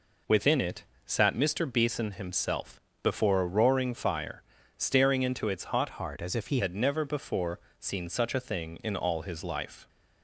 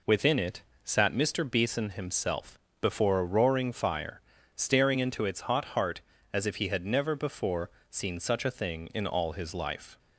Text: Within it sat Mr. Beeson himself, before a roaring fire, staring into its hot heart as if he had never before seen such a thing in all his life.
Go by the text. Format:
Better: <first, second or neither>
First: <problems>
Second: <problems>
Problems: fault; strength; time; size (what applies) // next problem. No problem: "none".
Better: second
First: pauses between "it" and "sat"; slight; at 0.8 s; 0.20 s long // changes voice from "heart" to "he"; from 5.9 to 6.6 s; 0.7 s long // pauses between "before" and "seen"; slight; at 7.5 s; 0.22 s long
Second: pauses between "it" and "sat"; slight; at 0.6 s; 0.20 s long // pauses between "before" and "seen"; slight; at 7.6 s; 0.22 s long